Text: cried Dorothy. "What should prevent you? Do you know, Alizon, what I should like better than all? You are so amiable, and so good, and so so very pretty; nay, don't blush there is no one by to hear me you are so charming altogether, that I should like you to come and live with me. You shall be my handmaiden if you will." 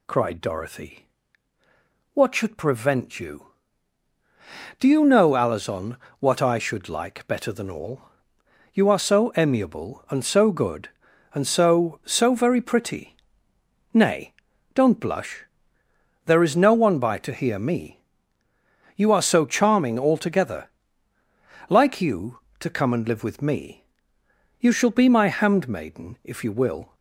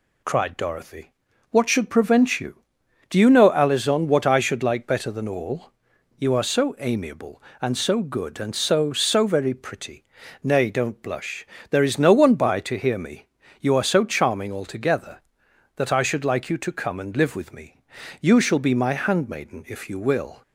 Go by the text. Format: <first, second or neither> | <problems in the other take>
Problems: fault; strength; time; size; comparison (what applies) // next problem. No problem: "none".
second | pauses between "blush" and "there"; noticeable; at 15.4 s; 0.84 s long; slight in the second // pauses between "me" and "you"; noticeable; at 18.0 s; 0.96 s long; slight in the second // skips "that I should"; at 21.1 s